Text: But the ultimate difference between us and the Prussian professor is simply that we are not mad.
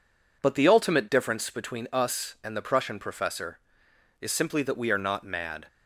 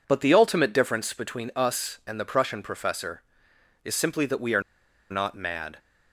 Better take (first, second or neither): first